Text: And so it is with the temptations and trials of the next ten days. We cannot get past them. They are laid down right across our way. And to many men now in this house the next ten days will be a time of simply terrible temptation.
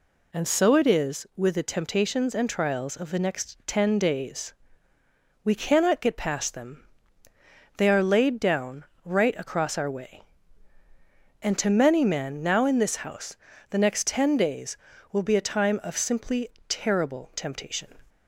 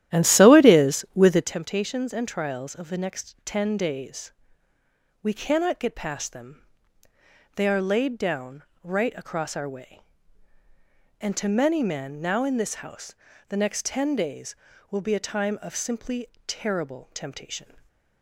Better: first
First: pauses between "down" and "right"; slight; at 8.8 s; 0.22 s long // pauses between "house" and "the"; slight; at 13.3 s; 0.34 s long // pauses between "simply" and "terrible"; slight; at 16.4 s; 0.18 s long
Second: starts louder than the rest; strong; until 1.6 s; 12 dB // pauses between "down" and "right"; slight; at 8.6 s; 0.22 s long // pauses between "house" and "the"; slight; at 13.1 s; 0.34 s long // pauses between "simply" and "terrible"; slight; at 16.2 s; 0.18 s long // stays silent after the last word; slight; from 17.6 s on; 0.6 s long

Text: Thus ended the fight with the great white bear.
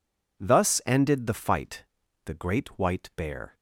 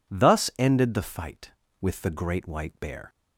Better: second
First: skips "with"; at 2.0 s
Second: none

